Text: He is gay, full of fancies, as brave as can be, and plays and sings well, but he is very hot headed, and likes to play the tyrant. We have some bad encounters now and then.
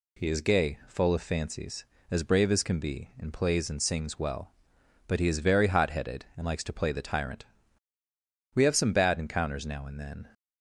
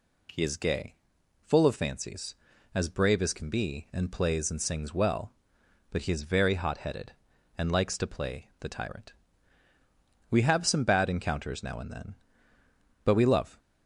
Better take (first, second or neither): first